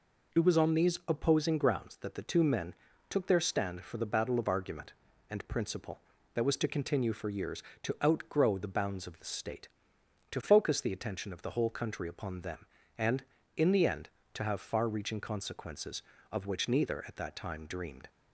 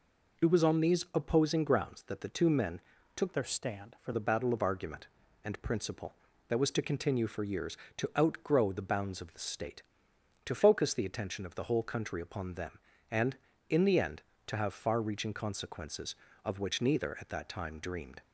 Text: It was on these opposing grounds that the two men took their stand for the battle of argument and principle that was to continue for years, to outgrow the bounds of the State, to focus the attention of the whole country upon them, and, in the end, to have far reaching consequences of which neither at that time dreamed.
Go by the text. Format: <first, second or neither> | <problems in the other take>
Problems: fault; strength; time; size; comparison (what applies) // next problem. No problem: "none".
first | pauses between "men" and "took"; slight; at 2.7 s; 0.36 s long; slight in the first // changes voice from "their" to "for"; from 3.3 to 4.1 s; 0.8 s long